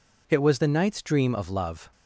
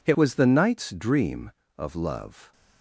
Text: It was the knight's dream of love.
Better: first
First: none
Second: changes voice at "was"; from 0.1 s on; 2.4 s long

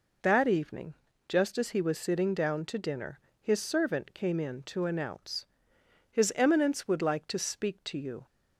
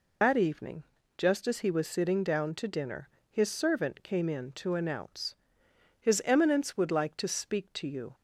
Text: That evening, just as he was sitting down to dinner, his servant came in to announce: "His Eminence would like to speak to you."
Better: first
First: none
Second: loses the start of "That"; at 0.2 s; 85 ms

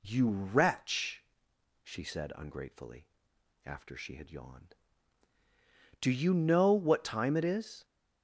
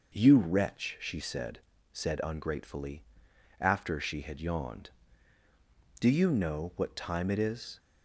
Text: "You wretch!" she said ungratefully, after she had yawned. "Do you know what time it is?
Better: first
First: none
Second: says "said" twice; at 1.9 s

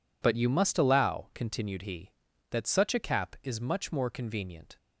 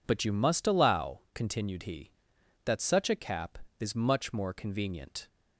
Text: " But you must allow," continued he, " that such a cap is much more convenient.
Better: neither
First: none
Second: none

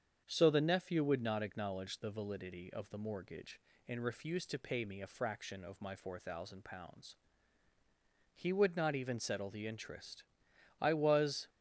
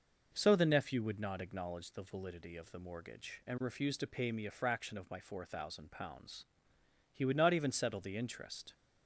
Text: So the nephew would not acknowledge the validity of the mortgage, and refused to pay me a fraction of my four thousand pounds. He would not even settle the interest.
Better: second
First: starts louder than the rest; strong; until 1.2 s; 7.5 dB // goes on to say "I was"; noticeable; from 10.8 s on; 0.68 s long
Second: none

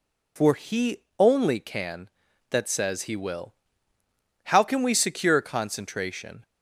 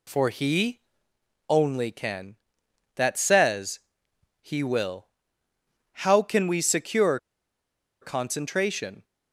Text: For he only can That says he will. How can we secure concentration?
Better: first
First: pauses between "he" and "only"; slight; at 0.9 s; 0.19 s long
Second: pauses between "he" and "only"; noticeable; at 0.7 s; 0.70 s long // pauses between "says" and "he"; noticeable; at 3.7 s; 0.60 s long // pauses between "secure" and "concentration"; noticeable; at 7.1 s; 0.83 s long

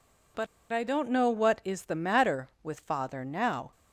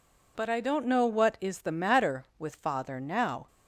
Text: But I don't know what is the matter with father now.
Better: second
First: pauses between "But" and "I"; slight; at 0.4 s; 0.26 s long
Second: none

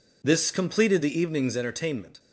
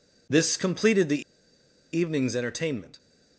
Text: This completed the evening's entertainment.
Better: first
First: none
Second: pauses between "the" and "evening's"; noticeable; at 1.2 s; 0.73 s long

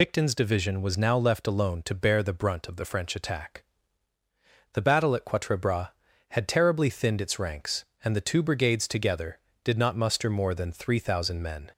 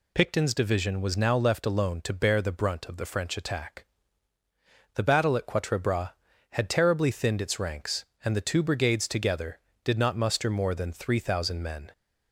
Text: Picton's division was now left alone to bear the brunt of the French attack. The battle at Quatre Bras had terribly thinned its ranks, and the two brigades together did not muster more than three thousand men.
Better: second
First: loses the start of "Picton's"; at 0.0 s; 45 ms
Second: none

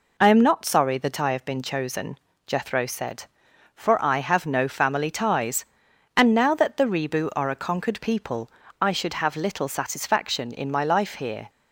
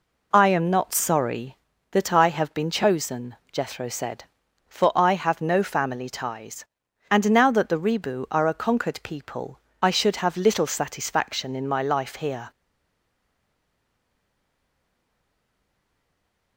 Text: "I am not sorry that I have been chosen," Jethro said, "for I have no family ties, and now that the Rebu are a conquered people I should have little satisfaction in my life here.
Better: first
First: pauses between "people" and "I"; slight; at 8.4 s; 0.32 s long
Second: pauses between "people" and "I"; slight; at 9.5 s; 0.24 s long // stays silent after the last word; strong; from 12.5 s on; 4.0 s long

